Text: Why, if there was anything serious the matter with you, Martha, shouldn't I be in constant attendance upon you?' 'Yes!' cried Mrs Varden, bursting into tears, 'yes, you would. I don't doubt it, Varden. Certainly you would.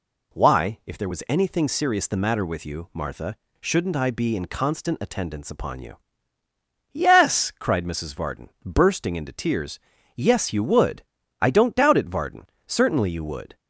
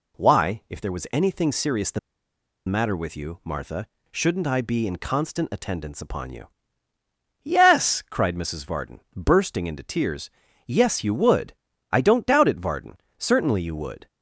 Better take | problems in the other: first | pauses between "the" and "matter"; noticeable; at 1.9 s; 0.68 s long

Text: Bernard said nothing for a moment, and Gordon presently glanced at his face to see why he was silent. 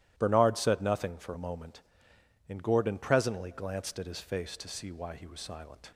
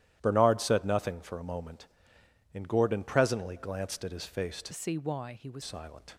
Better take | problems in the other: first | starts louder than the rest; strong; until 1.2 s; 12.5 dB; strong in the first // changes voice from "see" to "was"; from 4.7 to 5.6 s; 0.9 s long

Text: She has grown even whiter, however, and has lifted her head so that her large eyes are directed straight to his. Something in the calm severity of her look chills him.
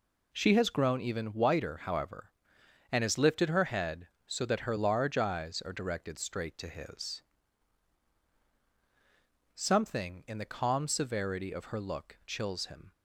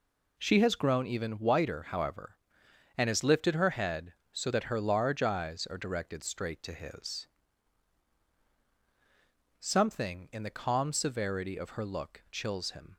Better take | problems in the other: neither | none

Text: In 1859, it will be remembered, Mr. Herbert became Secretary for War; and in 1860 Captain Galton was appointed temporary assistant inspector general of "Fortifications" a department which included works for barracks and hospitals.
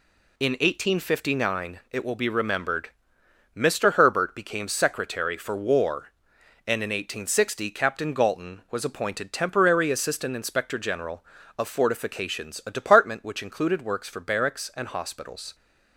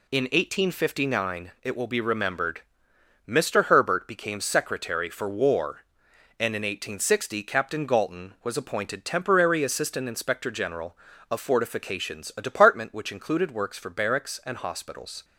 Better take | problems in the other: neither | none

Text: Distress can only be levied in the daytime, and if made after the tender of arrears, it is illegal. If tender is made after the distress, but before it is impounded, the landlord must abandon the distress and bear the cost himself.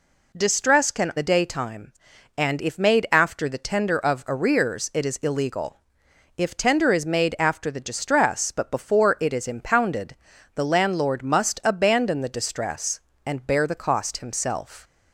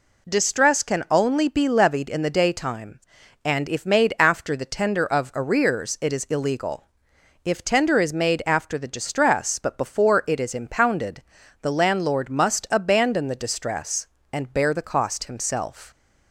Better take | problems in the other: second | skips "only be levied in"; at 1.1 s

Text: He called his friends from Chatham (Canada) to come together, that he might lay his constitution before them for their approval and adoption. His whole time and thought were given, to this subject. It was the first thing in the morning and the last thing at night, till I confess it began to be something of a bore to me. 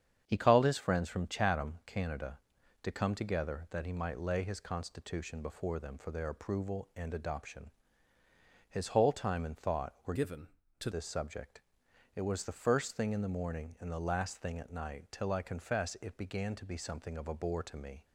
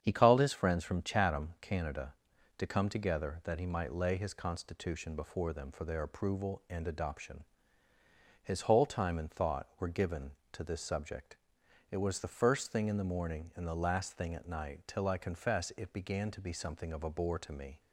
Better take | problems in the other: second | starts louder than the rest; strong; until 1.2 s; 8 dB; strong in the second // changes voice from "given" to "to"; from 10.1 to 10.8 s; 0.7 s long

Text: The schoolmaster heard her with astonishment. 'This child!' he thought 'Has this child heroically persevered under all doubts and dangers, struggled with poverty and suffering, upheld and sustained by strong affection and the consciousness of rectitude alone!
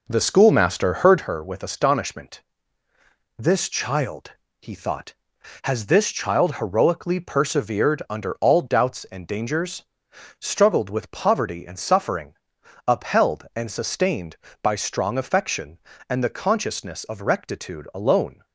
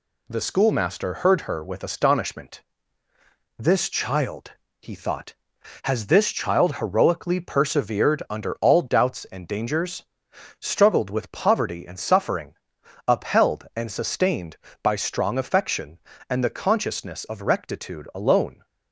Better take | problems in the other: second | starts louder than the rest; noticeable; until 1.3 s; 5 dB

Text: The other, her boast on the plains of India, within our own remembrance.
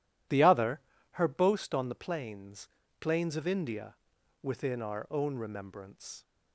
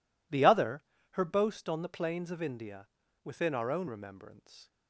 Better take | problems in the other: second | says "plains" twice; at 3.0 s

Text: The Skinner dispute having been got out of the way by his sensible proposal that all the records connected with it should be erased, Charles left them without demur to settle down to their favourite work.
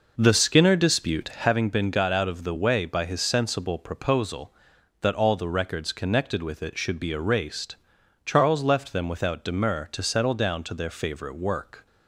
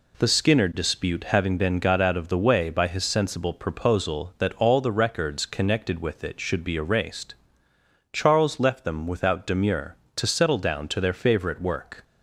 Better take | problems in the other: second | starts louder than the rest; noticeable; until 1.5 s; 5.5 dB

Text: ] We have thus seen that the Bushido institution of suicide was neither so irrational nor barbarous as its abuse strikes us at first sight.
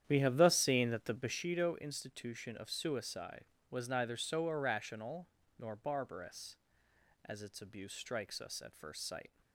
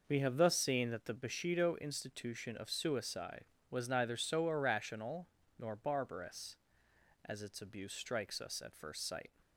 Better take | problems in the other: second | starts louder than the rest; strong; until 1.4 s; 10 dB // pauses between "irrational" and "nor"; slight; at 5.2 s; 0.30 s long; slight in the second

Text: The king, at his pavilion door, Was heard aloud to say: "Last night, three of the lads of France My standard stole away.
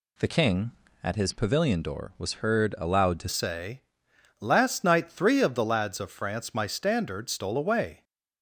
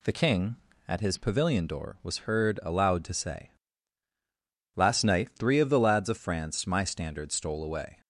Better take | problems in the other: second | changes voice at "say"; from 3.2 s on; 4.8 s long

